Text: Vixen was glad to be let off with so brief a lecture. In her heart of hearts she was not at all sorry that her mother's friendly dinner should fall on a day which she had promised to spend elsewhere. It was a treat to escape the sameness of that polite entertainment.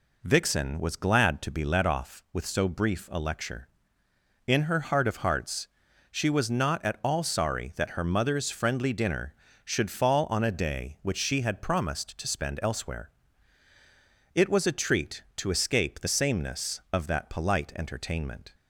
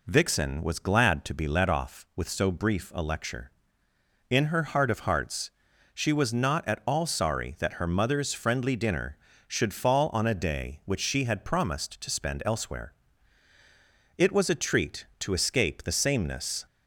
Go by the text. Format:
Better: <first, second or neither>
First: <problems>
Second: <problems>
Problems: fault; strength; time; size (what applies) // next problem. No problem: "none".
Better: first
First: pauses between "hearts" and "she"; at 5.6 s; 0.44 s long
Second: pauses between "hearts" and "she"; at 5.4 s; 0.44 s long // stops before "of that polite entertainment"; at 16.6 s